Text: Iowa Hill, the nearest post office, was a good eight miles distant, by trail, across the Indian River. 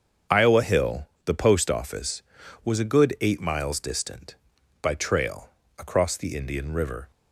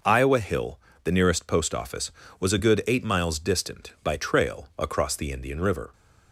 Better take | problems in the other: second | starts louder than the rest; until 1.4 s; 7 dB // skips "nearest"; at 1.3 s

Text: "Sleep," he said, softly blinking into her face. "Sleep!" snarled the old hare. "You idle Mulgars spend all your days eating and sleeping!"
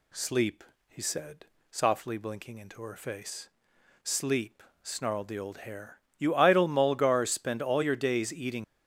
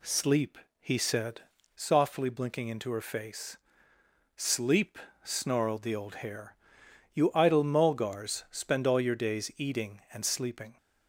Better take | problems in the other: second | stops before "and sleeping"; at 8.6 s

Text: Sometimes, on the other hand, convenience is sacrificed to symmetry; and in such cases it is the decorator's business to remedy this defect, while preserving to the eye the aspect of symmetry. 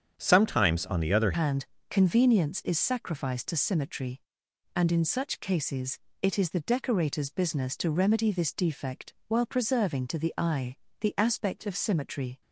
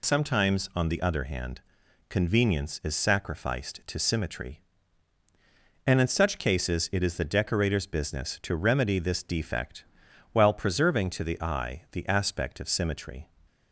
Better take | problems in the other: second | starts louder than the rest; strong; until 1.1 s; 8 dB // changes voice at "hand"; from 1.3 s on; 11.1 s long // pauses between "cases" and "it"; slight; at 5.9 s; 0.22 s long // pauses between "eye" and "the"; slight; at 10.7 s; 0.24 s long

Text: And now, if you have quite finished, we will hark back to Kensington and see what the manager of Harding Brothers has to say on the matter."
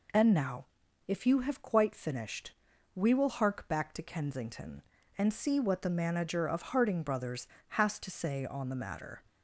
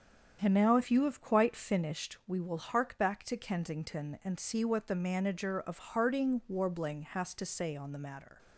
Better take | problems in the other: first | starts louder than the rest; strong; until 1.4 s; 8 dB // says "Warbling" for "Brothers"; at 6.4 s

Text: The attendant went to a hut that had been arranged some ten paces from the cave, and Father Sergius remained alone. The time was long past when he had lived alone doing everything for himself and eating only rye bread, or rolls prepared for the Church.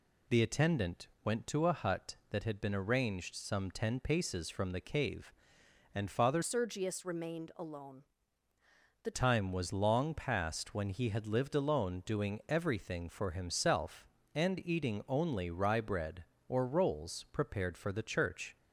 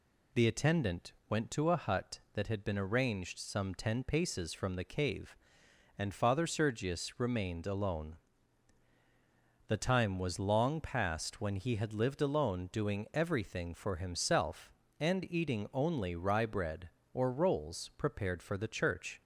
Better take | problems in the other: second | pauses between "attendant" and "went"; slight; at 1.0 s; 0.16 s long; slight in the second // changes voice from "Sergius" to "The"; from 6.4 to 9.1 s; 2.7 s long

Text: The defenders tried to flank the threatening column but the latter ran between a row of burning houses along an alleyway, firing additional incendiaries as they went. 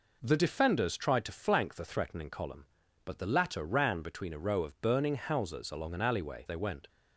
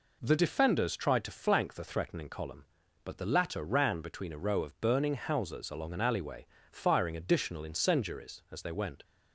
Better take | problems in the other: second | skips "firing additional incendiaries as"; at 6.4 s

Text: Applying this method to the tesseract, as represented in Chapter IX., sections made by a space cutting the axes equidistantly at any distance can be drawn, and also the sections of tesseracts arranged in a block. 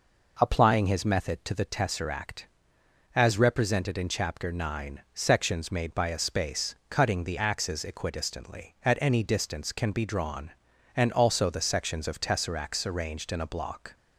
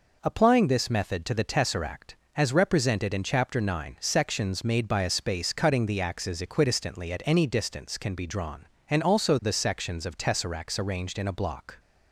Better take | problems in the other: second | says "his" for "this"; at 0.8 s

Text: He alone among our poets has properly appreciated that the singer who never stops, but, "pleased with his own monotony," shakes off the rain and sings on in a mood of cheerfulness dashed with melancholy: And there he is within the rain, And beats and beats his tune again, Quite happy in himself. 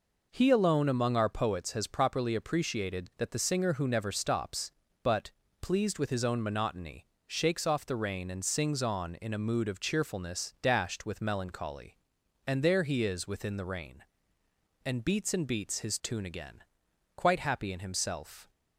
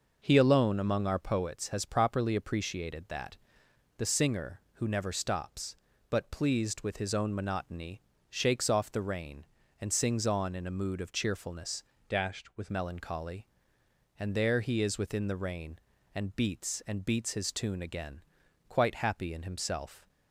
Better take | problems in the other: first | pauses between "that" and "the"; noticeable; at 3.3 s; 0.62 s long // changes voice from "dashed" to "with"; from 12.0 to 12.7 s; 0.7 s long

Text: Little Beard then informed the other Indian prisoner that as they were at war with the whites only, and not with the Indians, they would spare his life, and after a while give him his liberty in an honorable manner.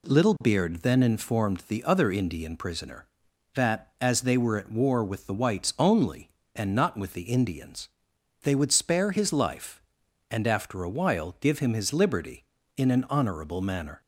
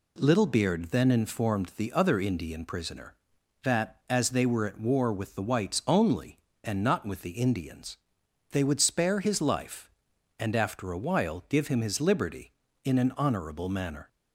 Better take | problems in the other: neither | none

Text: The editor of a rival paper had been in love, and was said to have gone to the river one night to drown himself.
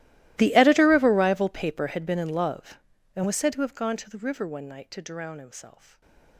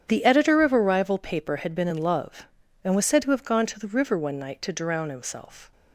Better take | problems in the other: second | gets quieter; strong; throughout; 25.5 dB // starts louder than the rest; strong; until 1.3 s; 16 dB; strong in the second

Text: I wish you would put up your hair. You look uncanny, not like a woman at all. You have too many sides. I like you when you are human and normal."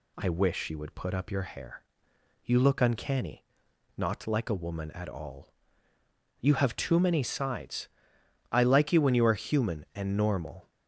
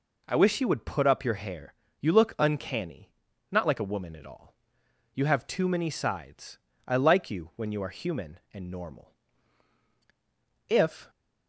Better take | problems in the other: first | goes on to say "If"; slight; from 10.6 s on; 0.42 s long

